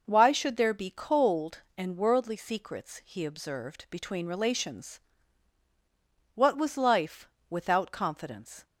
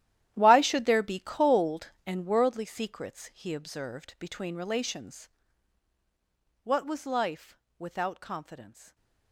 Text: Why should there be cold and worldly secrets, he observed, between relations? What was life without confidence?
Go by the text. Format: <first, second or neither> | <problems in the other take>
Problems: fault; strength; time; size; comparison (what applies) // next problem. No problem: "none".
first | gets quieter; strong; throughout; 15 dB // pauses between "life" and "without"; slight; at 7.5 s; 0.22 s long; slight in the first